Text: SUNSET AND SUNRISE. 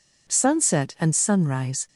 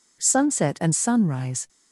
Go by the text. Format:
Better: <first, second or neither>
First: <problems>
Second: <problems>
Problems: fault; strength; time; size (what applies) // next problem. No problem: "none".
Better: neither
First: none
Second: none